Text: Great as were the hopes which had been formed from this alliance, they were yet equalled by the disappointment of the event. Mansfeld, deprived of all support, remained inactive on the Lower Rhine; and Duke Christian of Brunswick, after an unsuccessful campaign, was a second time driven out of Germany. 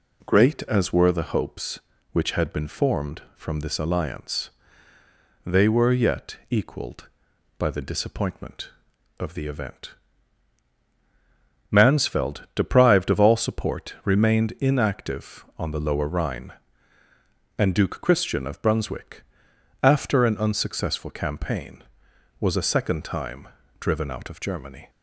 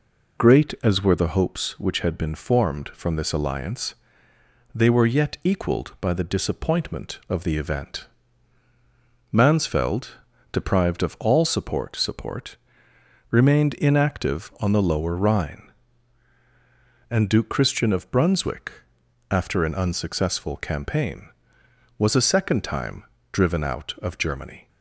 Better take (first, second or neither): first